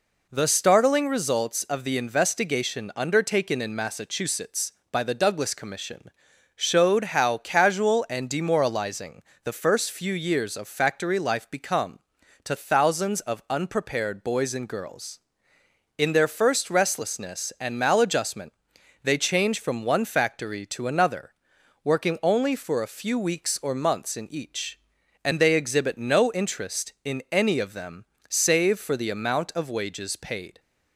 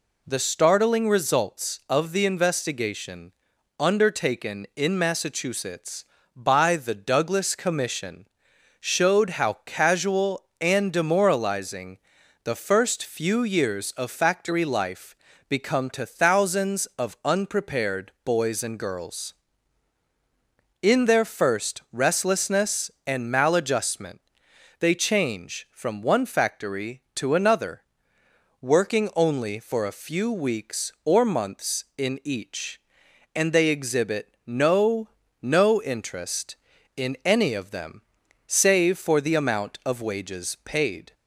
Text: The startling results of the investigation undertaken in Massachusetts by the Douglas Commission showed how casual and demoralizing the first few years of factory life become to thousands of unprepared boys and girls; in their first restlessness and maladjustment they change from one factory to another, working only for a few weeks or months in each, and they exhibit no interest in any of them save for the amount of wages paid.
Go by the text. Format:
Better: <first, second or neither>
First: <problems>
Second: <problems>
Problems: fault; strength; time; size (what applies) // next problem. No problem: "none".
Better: first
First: pauses between "Commission" and "showed"; at 6.0 s; 0.44 s long // pauses between "demoralizing" and "the"; slight; at 9.2 s; 0.22 s long // pauses between "maladjustment" and "they"; noticeable; at 18.5 s; 0.50 s long // pauses between "them" and "save"; slight; at 28.0 s; 0.26 s long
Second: pauses between "investigation" and "undertaken"; at 3.3 s; 0.44 s long // pauses between "Commission" and "showed"; noticeable; at 8.2 s; 0.50 s long // pauses between "demoralizing" and "the"; noticeable; at 11.9 s; 0.48 s long // pauses between "life" and "become"; slight; at 15.1 s; 0.36 s long // pauses between "maladjustment" and "they"; noticeable; at 24.1 s; 0.60 s long // says "no" twice; at 35.4 s // pauses between "them" and "save"; noticeable; at 38.0 s; 0.46 s long